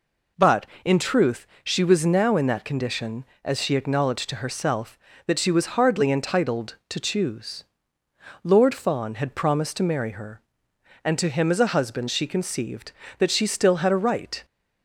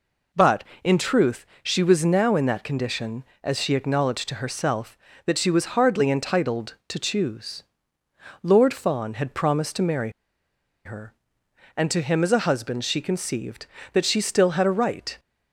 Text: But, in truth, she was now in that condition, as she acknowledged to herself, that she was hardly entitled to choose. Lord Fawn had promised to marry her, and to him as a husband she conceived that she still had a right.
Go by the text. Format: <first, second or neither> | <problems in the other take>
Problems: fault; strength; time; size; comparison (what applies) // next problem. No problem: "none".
first | pauses between "marry" and "her"; noticeable; at 10.1 s; 0.75 s long